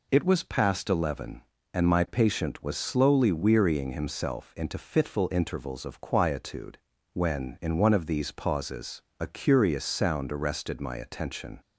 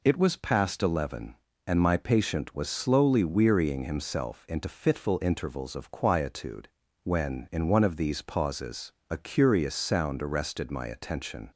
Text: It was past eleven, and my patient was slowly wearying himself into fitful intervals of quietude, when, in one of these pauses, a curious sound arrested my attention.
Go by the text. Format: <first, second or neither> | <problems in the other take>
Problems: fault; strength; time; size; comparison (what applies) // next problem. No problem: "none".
neither | none